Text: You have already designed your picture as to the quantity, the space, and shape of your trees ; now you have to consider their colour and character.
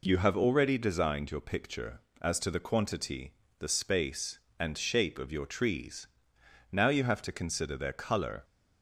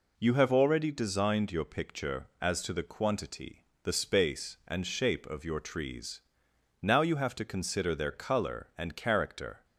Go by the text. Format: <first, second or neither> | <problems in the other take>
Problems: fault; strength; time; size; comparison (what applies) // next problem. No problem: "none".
second | stops before "and character"; at 8.4 s